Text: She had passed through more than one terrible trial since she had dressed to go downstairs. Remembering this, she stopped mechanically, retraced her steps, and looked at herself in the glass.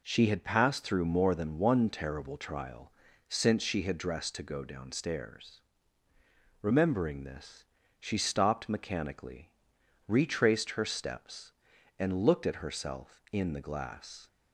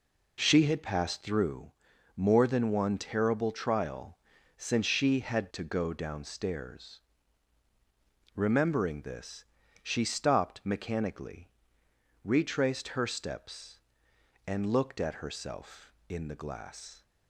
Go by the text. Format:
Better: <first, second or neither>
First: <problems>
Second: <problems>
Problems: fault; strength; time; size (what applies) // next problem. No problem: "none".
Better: first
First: pauses between "trial" and "since"; at 2.9 s; 0.38 s long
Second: pauses between "through" and "more"; at 1.7 s; 0.42 s long // pauses between "trial" and "since"; at 4.1 s; 0.40 s long // skips "dressed"; at 5.5 s